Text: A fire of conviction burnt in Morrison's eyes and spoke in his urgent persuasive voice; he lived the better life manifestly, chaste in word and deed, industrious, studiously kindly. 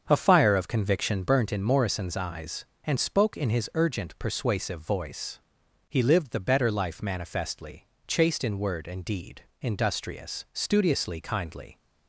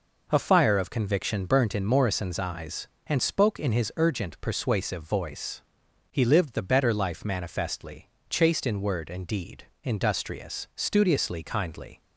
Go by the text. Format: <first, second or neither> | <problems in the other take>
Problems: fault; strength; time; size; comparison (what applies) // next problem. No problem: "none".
second | starts louder than the rest; strong; until 1.3 s; 7 dB